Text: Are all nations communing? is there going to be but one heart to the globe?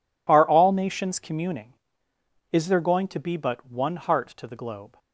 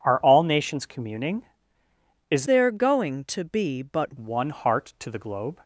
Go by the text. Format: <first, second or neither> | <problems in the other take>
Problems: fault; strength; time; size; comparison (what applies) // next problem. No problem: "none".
first | changes voice from "there" to "but"; from 2.4 to 4.1 s; 1.7 s long